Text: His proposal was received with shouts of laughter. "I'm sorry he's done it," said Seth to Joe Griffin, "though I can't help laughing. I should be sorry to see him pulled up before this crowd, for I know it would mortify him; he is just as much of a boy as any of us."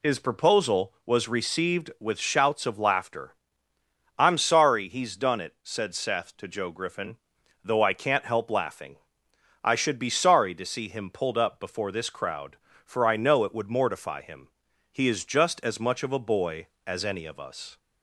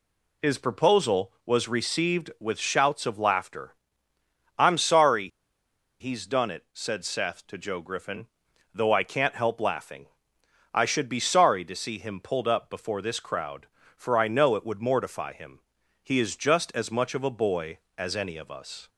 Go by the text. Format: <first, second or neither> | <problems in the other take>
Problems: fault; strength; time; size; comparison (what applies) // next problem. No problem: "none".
first | pauses between "sorry" and "he's"; noticeable; at 5.2 s; 0.72 s long